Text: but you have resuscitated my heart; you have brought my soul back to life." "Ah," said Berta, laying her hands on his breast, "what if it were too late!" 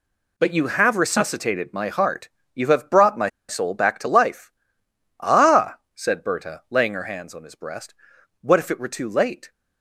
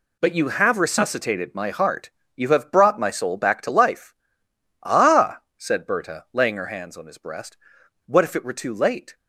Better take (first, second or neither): second